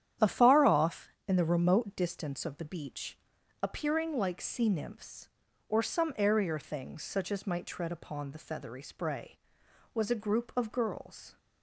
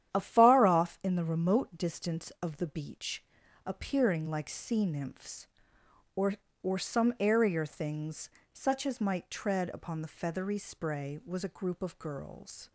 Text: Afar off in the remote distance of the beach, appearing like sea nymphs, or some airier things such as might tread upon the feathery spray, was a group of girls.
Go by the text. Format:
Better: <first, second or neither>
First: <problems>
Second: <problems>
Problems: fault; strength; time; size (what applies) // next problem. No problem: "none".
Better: first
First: starts louder than the rest; strong; until 1.4 s; 10 dB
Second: starts louder than the rest; strong; until 1.1 s; 10.5 dB // says "or" twice; at 6.6 s // pauses between "things" and "such"; slight; at 8.3 s; 0.20 s long